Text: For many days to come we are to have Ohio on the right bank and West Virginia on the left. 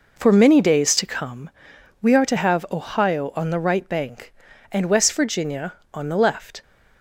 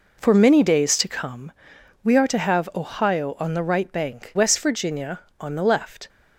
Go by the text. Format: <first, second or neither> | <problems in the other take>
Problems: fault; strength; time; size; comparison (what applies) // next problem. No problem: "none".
first | pauses between "come" and "we"; noticeable; at 1.5 s; 0.50 s long; noticeable in the first // skips "and"; at 4.3 s